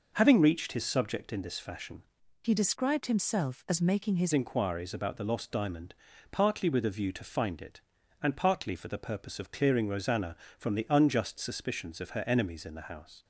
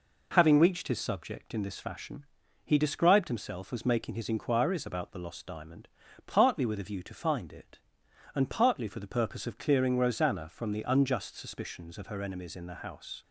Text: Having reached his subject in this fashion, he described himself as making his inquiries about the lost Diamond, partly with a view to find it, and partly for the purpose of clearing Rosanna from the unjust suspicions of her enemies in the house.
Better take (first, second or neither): second